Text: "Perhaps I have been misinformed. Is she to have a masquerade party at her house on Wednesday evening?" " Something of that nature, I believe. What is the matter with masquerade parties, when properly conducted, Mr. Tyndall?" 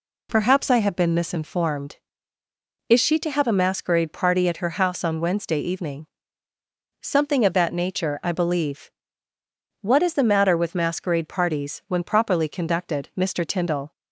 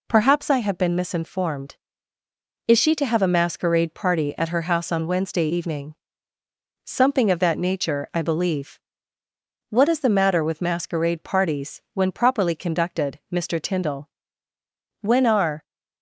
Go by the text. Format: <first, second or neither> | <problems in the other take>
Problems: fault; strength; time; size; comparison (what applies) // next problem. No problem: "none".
first | goes on to say "When are"; noticeable; from 14.9 s on; 0.64 s long